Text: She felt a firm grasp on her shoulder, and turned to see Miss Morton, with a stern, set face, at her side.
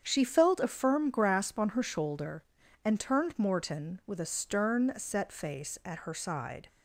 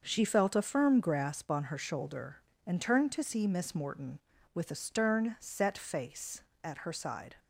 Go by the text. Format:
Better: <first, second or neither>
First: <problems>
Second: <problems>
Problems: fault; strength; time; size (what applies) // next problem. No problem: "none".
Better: second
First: starts louder than the rest; strong; until 1.0 s; 7.5 dB // skips "to see Miss"; at 3.3 s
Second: starts louder than the rest; until 1.0 s; 6 dB